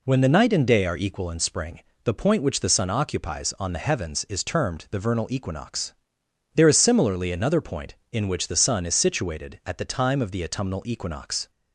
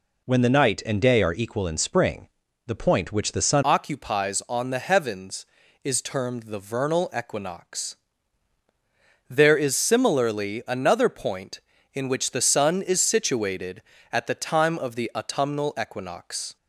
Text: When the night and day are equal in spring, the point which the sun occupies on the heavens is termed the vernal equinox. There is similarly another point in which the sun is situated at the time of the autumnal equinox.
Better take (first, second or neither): first